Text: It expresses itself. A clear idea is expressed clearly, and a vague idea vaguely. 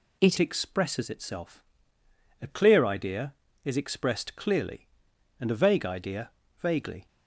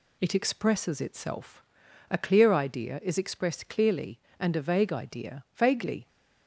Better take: second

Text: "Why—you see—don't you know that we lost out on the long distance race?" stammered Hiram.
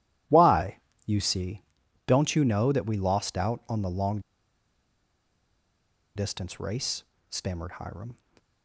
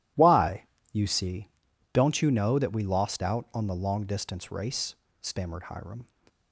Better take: second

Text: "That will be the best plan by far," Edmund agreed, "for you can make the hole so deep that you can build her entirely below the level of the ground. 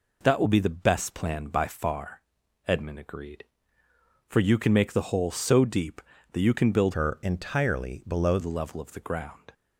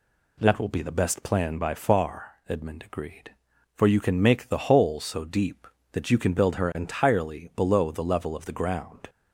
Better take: second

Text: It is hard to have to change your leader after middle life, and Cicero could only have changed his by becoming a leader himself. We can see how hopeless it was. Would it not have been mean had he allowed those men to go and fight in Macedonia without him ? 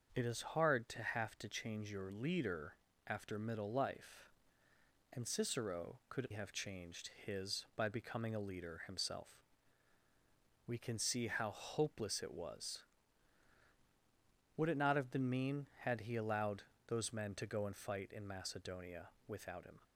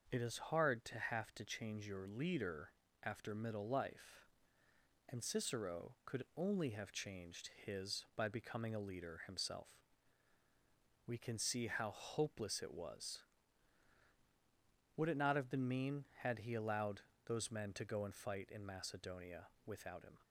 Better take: second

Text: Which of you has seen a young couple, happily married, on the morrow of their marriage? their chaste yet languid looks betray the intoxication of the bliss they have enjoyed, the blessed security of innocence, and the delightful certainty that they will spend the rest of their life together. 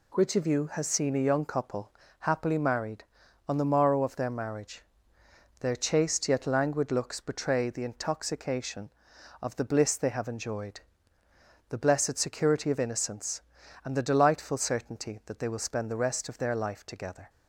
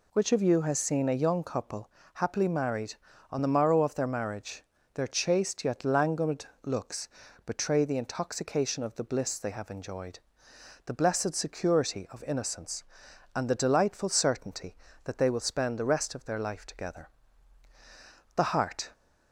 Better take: first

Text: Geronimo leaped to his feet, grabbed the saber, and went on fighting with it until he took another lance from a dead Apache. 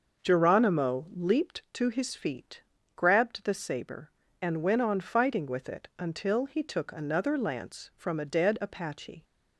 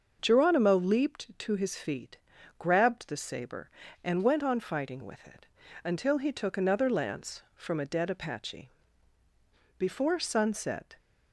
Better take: first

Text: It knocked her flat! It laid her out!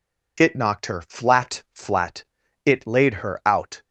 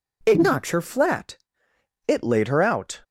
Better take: second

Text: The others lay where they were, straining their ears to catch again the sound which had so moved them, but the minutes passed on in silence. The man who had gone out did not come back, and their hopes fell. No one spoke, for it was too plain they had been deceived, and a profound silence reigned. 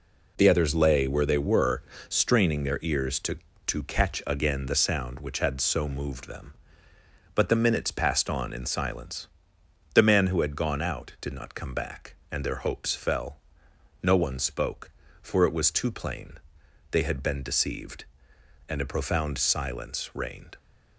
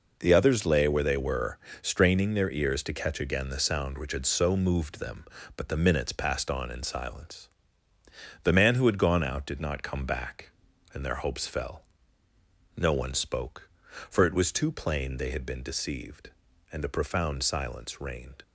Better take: second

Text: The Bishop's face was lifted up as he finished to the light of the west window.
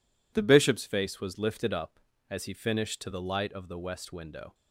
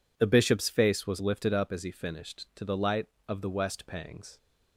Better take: first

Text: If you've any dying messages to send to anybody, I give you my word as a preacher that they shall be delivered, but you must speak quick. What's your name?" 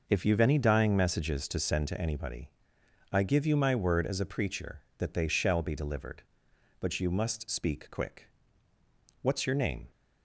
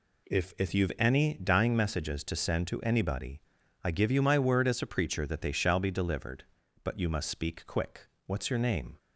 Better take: first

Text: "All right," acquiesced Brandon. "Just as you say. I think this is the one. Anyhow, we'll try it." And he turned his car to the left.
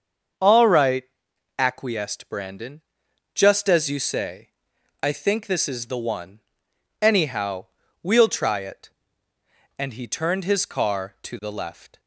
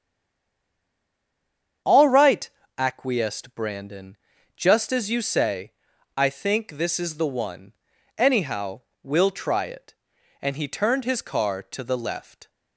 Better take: first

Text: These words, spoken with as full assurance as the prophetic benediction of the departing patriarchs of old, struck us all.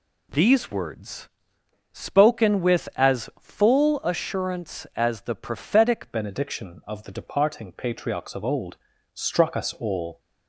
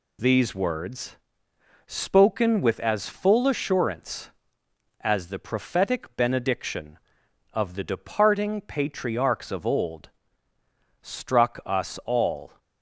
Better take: second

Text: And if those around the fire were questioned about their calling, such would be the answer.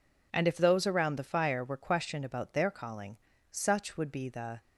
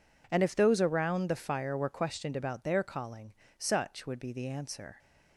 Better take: second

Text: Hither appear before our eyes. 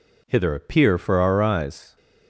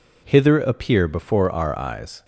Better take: second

